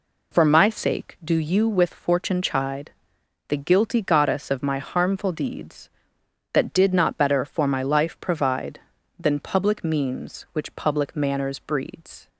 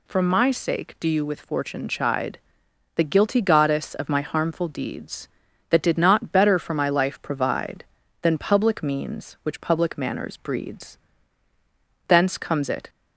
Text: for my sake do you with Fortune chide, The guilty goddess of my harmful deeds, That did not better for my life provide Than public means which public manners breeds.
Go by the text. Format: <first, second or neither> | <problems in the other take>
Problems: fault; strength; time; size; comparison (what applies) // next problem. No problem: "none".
first | goes on to say "Thence comes it"; noticeable; from 12.0 s on; 0.82 s long